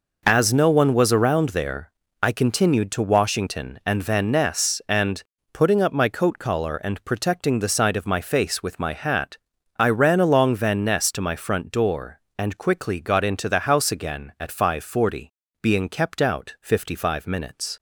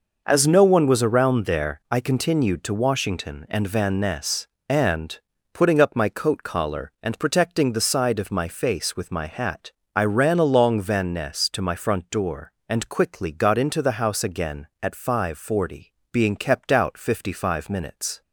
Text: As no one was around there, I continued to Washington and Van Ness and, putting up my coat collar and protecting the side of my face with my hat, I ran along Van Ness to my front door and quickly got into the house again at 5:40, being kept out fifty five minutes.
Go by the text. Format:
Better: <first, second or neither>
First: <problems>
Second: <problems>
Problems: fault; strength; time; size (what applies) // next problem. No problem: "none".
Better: neither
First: none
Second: none